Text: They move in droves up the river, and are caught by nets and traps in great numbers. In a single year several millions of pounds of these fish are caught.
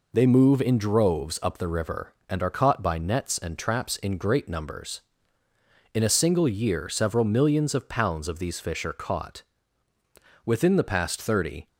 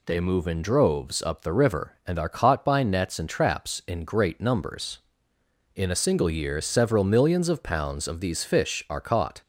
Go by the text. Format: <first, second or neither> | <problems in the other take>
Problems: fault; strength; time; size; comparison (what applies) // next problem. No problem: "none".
second | goes on to say "Within the past thirty"; noticeable; from 10.4 s on; 1.2 s long